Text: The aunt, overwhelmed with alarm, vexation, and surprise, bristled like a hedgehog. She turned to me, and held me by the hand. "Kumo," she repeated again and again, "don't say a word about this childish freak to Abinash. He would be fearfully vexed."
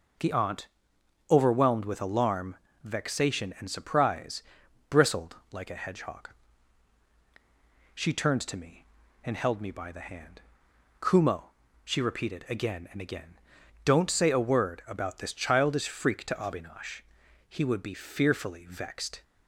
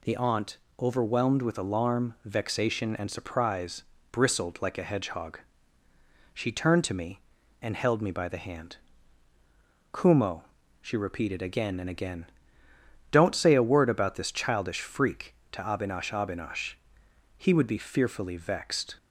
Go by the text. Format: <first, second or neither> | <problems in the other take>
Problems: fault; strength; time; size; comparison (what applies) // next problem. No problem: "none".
first | says "Abinash" twice; at 16.1 s